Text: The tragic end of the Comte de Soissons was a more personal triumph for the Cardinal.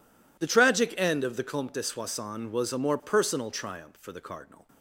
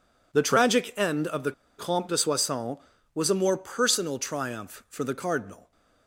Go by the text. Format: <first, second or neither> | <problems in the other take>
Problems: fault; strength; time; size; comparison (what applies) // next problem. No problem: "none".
first | pauses between "the" and "Comte"; slight; at 1.5 s; 0.26 s long